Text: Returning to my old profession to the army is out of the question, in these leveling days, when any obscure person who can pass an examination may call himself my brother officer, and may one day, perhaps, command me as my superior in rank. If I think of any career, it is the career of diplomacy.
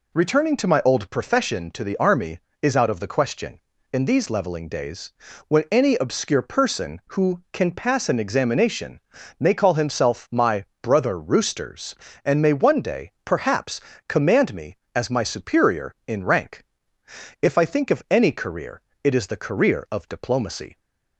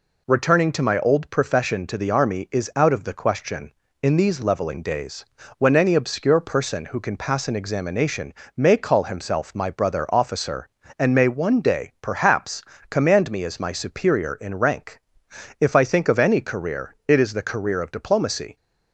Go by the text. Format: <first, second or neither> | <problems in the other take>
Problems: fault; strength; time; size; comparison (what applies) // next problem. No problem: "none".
second | pauses between "examination" and "may"; at 9.0 s; 0.38 s long; slight in the second // pauses between "my" and "brother"; slight; at 10.6 s; 0.16 s long // says "roosters" for "officer"; at 11.2 s